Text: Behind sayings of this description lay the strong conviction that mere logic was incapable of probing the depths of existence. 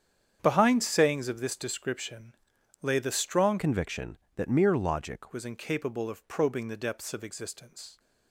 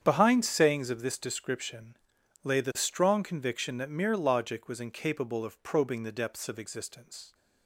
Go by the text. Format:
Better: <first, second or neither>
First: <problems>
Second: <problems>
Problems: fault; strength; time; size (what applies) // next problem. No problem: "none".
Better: second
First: starts louder than the rest; strong; until 1.4 s; 8.5 dB // pauses between "description" and "lay"; noticeable; at 2.3 s; 0.48 s long // changes voice from "conviction" to "logic"; from 3.5 to 5.3 s; 1.8 s long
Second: starts louder than the rest; strong; until 1.0 s; 8.5 dB // pauses between "description" and "lay"; noticeable; at 1.9 s; 0.48 s long